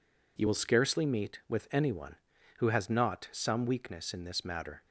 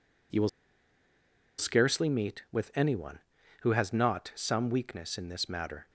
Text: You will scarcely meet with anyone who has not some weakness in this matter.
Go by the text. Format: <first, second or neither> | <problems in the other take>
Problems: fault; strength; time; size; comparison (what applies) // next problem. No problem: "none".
first | pauses between "will" and "scarcely"; at 0.4 s; 1.0 s long